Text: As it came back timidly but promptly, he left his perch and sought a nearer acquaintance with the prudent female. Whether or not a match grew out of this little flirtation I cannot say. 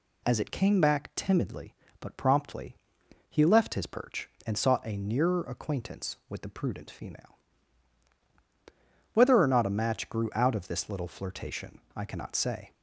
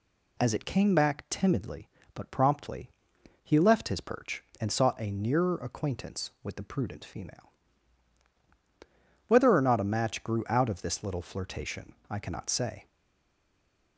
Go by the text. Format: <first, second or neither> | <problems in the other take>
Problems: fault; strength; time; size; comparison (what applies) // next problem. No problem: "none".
first | pauses between "flirtation" and "I"; slight; at 11.9 s; 0.16 s long; slight in the first // stays silent after the last word; from 12.8 s on; 1.1 s long